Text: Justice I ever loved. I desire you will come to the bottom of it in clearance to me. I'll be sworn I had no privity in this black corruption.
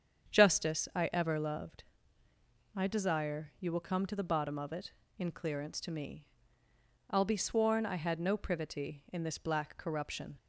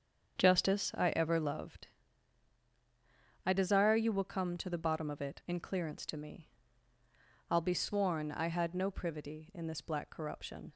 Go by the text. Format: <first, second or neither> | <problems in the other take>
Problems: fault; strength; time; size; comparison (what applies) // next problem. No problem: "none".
neither | starts louder than the rest; strong; the same in both